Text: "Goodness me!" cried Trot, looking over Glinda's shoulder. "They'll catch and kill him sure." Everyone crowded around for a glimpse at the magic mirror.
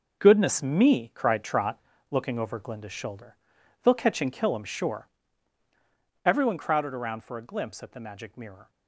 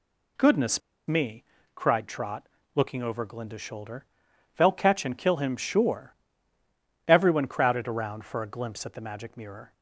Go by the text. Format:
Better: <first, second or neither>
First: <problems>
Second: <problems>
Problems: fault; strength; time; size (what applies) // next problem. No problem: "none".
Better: first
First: none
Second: pauses between "Goodness" and "me"; slight; at 0.8 s; 0.28 s long